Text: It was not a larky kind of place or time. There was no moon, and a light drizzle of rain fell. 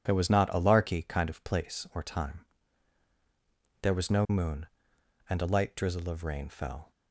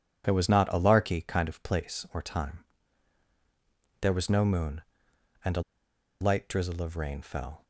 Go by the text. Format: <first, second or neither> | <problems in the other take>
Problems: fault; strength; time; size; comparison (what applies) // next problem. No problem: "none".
first | pauses between "a" and "light"; noticeable; at 5.6 s; 0.59 s long